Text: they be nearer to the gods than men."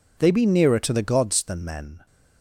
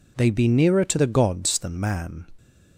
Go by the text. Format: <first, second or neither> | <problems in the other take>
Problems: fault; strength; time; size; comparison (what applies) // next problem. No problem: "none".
first | says "man" for "men"; at 1.7 s